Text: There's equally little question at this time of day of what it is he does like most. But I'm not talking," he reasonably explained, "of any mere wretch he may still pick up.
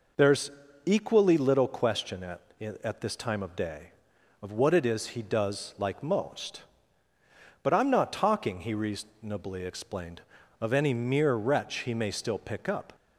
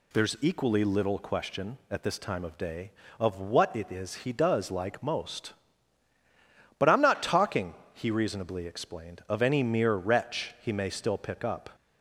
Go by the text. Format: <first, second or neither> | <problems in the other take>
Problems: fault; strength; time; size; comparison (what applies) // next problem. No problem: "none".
second | pauses between "There's" and "equally"; slight; at 0.5 s; 0.34 s long // says "at" twice; at 2.8 s